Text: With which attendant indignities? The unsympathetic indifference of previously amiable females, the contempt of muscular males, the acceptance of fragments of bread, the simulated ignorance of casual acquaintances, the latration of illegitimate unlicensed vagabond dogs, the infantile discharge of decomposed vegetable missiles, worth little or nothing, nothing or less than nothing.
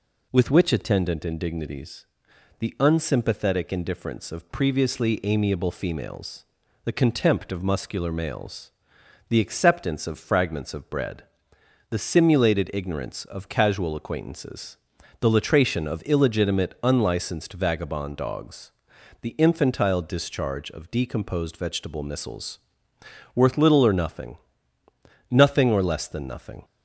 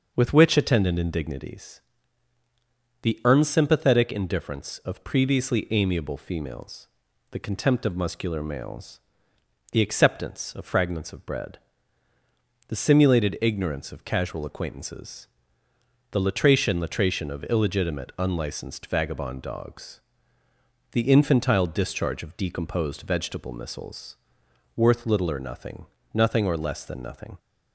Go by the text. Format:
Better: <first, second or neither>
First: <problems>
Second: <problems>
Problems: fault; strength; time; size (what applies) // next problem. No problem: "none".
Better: first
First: none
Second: starts louder than the rest; until 1.1 s; 6 dB // says "latration" twice; at 16.7 s